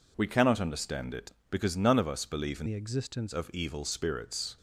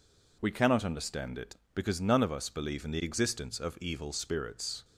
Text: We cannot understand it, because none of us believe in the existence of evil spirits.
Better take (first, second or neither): second